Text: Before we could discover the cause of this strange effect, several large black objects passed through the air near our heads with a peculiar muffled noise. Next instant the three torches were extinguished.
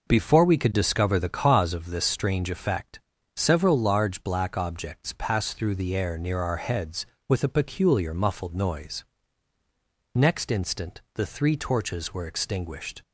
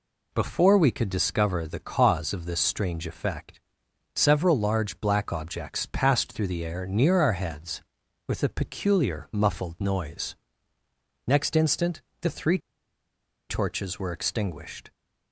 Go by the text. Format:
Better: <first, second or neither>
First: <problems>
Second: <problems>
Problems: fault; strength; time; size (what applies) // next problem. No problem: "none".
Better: first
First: none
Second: pauses between "instant" and "the"; slight; at 12.0 s; 0.20 s long // pauses between "three" and "torches"; noticeable; at 12.5 s; 0.91 s long